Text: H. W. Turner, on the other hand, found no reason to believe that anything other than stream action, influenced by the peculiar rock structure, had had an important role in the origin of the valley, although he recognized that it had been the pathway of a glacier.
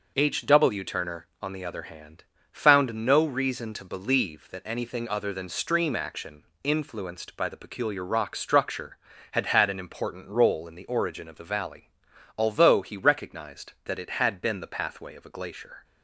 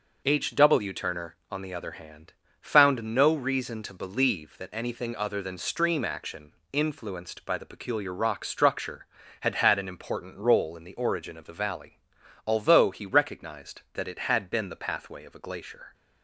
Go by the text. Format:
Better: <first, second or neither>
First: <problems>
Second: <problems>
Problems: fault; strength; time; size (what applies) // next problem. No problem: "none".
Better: neither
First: none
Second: none